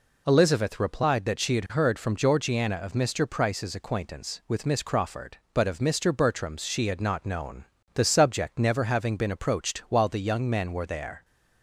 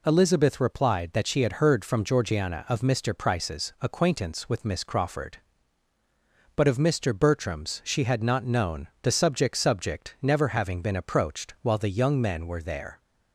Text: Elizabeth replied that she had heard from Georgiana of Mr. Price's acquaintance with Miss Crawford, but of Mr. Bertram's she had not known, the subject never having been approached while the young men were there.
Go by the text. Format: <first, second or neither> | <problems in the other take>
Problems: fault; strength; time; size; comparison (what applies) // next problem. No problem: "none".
first | says "subject" twice; at 9.5 s